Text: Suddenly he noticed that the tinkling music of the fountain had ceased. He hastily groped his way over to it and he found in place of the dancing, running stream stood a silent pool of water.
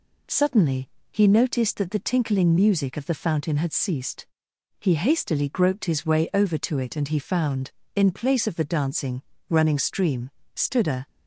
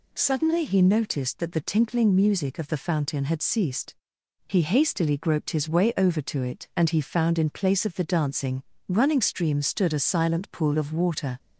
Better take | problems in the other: second | pauses between "Suddenly" and "he"; slight; at 0.8 s; 0.22 s long // pauses between "stream" and "stood"; slight; at 10.3 s; 0.24 s long // stops before "silent pool of water"; at 11.0 s

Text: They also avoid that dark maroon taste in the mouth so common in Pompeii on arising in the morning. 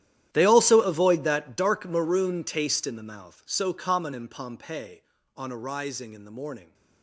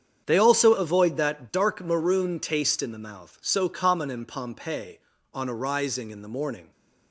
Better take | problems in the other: second | gets quieter; strong; throughout; 18.5 dB // starts louder than the rest; strong; until 1.3 s; 11.5 dB; strong in the second

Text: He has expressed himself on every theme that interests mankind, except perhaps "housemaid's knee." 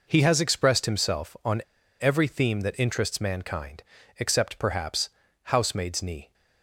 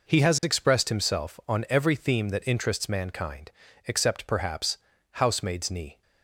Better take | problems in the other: second | pauses between "on" and "every"; at 1.6 s; 0.41 s long // pauses between "perhaps" and "housemaid's"; at 5.0 s; 0.38 s long; also in the second

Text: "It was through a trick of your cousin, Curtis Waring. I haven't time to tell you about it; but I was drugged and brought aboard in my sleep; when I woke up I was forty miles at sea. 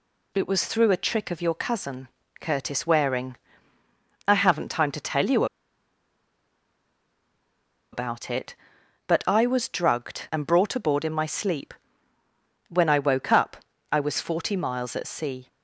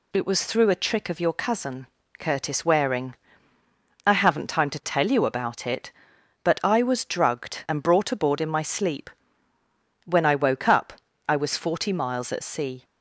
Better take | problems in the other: second | pauses between "you" and "about"; strong; at 5.4 s; 2.4 s long // pauses between "up" and "I"; slight; at 13.5 s; 0.36 s long; slight in the second

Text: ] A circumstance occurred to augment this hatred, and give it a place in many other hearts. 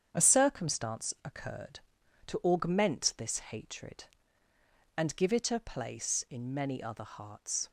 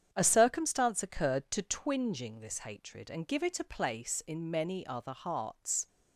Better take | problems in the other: first | starts louder than the rest; strong; until 1.1 s; 8.5 dB; strong in the first // says "twinging" for "augment"; at 1.6 s

